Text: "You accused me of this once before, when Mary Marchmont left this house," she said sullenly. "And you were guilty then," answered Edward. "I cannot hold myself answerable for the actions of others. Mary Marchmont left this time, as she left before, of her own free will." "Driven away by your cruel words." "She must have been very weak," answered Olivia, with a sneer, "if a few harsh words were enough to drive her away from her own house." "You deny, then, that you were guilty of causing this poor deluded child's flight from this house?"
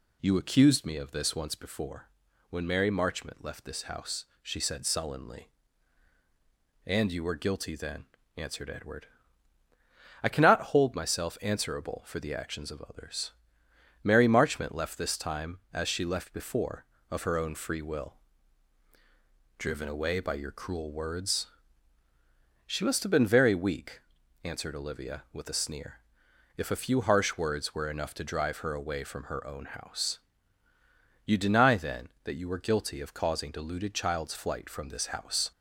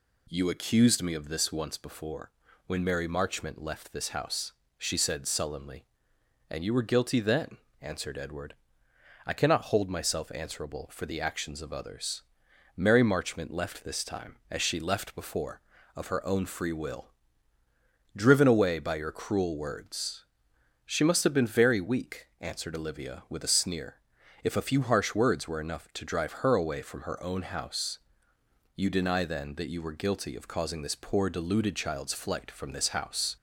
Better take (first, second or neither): second